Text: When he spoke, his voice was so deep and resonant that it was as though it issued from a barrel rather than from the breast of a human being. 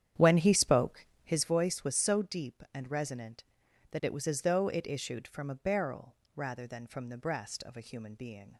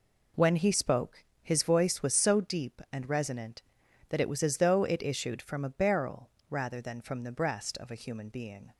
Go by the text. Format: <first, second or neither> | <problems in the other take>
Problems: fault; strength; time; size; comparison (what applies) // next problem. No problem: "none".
second | starts louder than the rest; strong; until 1.4 s; 9.5 dB // pauses between "barrel" and "rather"; slight; at 6.1 s; 0.22 s long; slight in the second